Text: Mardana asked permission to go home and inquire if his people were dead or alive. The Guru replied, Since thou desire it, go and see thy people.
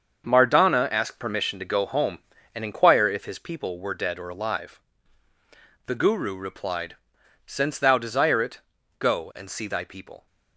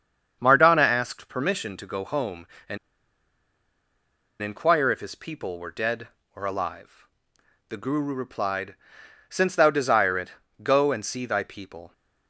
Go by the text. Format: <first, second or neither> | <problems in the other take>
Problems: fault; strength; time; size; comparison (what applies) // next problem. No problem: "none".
first | starts louder than the rest; strong; until 1.4 s; 7 dB; also in the first // pauses between "and" and "inquire"; strong; at 2.7 s; 1.6 s long